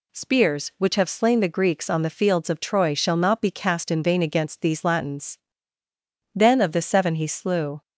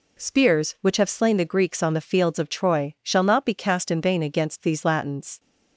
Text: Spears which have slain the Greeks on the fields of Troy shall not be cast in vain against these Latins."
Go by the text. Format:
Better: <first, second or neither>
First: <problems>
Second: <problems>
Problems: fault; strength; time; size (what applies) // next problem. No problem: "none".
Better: second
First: goes on to say "Then of the seven he slew"; from 6.3 s on; 1.4 s long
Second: none